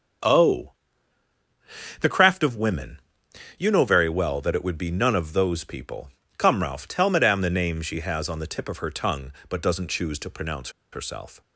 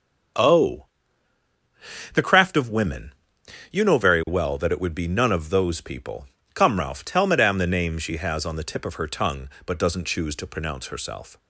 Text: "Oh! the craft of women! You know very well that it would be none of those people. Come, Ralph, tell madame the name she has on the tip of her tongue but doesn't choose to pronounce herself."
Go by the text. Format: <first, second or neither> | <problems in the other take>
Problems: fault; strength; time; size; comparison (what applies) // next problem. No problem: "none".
second | starts louder than the rest; until 2.5 s; 7 dB; also in the second // pauses between "pronounce" and "herself"; slight; at 10.7 s; 0.21 s long